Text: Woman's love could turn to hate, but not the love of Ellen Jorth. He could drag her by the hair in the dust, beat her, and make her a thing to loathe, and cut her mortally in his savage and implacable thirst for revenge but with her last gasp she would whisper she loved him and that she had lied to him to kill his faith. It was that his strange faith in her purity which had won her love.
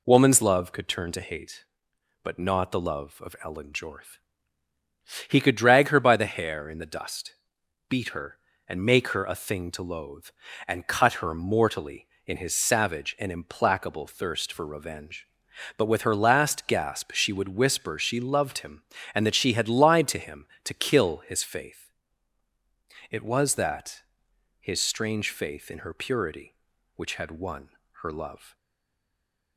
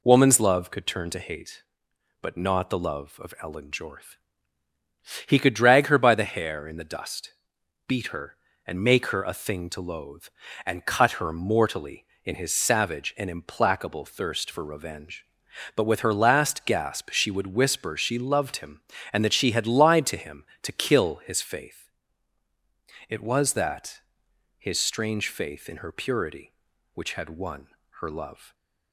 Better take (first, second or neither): second